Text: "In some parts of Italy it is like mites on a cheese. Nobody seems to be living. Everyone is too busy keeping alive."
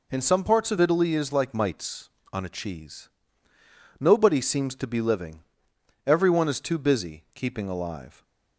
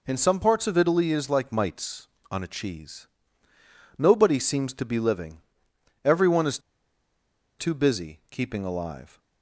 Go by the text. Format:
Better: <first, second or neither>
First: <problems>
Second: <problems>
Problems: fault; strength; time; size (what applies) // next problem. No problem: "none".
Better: first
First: none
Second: pauses between "is" and "too"; at 6.5 s; 1.0 s long